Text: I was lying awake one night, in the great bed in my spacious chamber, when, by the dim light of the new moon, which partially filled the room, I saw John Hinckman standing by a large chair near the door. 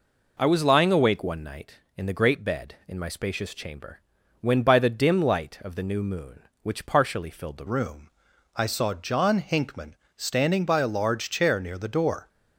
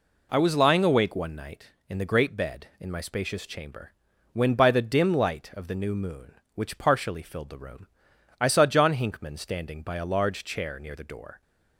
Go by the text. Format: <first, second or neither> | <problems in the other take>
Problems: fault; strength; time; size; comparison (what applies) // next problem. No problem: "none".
second | changes voice at "room"; from 7.6 s on; 4.6 s long // pauses between "Hinckman" and "standing"; slight; at 9.9 s; 0.22 s long